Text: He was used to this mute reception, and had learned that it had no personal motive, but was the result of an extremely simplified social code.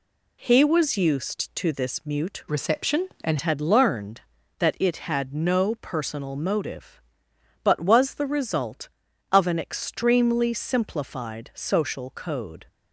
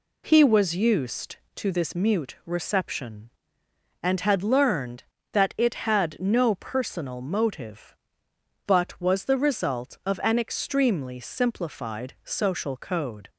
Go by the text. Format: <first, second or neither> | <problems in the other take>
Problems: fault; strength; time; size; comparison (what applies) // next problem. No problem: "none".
second | changes voice from "reception" to "and"; from 2.4 to 3.3 s; 0.9 s long